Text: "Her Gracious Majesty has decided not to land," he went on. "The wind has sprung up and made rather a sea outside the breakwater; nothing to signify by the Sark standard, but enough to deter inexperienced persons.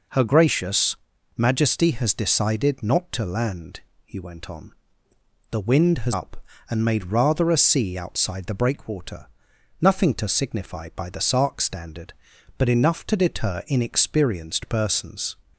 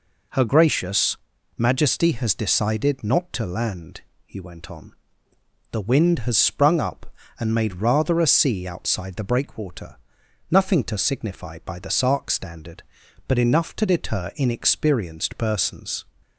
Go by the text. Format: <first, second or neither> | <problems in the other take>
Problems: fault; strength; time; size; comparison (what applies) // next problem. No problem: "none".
second | pauses between "Gracious" and "Majesty"; at 0.9 s; 0.40 s long; also in the second // skips "sprung"; at 6.1 s